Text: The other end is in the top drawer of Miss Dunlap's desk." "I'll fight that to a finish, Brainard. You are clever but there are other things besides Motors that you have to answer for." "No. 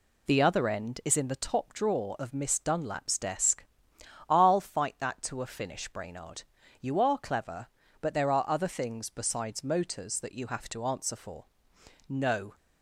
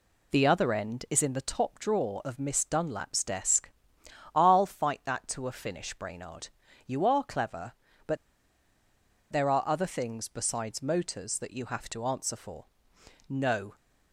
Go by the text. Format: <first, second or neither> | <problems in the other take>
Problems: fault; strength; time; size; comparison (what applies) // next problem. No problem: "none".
first | pauses between "but" and "there"; at 8.1 s; 1.1 s long